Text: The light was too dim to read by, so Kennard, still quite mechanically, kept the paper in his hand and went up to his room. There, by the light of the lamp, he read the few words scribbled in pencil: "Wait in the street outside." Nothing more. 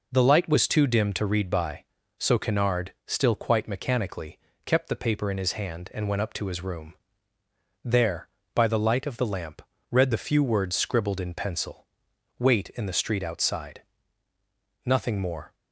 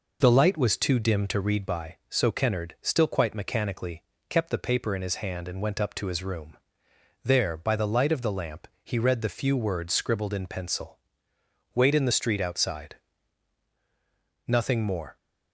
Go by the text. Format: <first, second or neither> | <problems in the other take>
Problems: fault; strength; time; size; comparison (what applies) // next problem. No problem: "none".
second | skips "he"; at 9.7 s